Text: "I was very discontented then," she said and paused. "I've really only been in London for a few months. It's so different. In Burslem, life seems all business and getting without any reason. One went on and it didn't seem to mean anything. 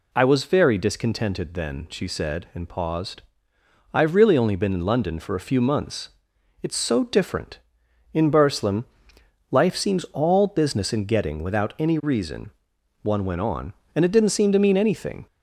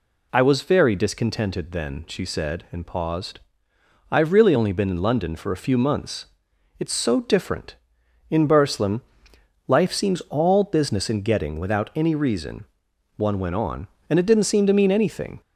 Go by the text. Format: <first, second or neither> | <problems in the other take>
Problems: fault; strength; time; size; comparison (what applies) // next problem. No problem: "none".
neither | none